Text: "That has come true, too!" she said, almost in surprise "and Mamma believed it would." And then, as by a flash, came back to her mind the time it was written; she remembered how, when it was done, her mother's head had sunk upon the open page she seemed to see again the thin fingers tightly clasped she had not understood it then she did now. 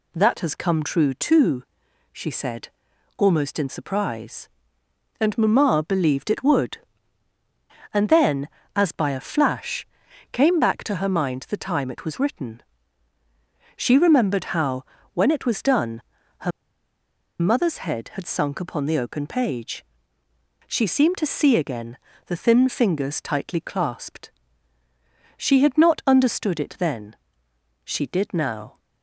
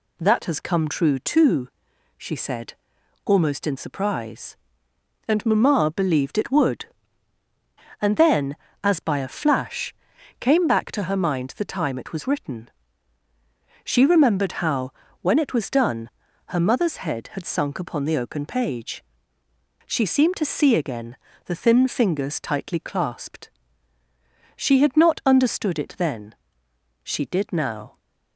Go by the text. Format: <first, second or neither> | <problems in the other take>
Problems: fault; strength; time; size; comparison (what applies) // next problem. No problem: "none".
second | pauses between "her" and "mother's"; noticeable; at 16.5 s; 0.89 s long // pauses between "page" and "she"; noticeable; at 19.8 s; 0.86 s long; noticeable in the second // pauses between "again" and "the"; slight; at 21.9 s; 0.30 s long; slight in the second // pauses between "clasped" and "she"; at 24.3 s; 1.0 s long; also in the second // pauses between "then" and "she"; noticeable; at 27.1 s; 0.70 s long; noticeable in the second